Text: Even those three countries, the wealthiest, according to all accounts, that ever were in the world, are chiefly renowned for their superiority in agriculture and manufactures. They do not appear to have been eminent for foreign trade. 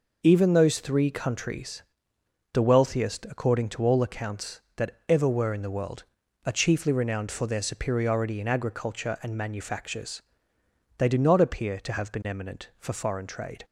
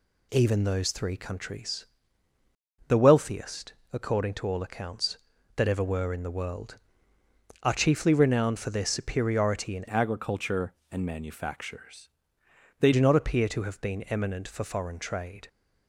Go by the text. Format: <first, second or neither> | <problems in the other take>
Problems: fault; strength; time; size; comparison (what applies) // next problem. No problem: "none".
first | changes voice from "agriculture" to "They"; from 9.8 to 12.9 s; 3.1 s long